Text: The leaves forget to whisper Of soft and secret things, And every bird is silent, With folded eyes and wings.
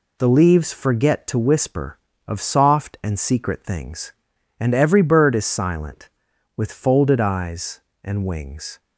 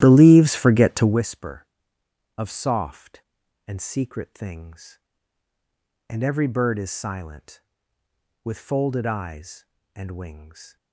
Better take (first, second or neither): first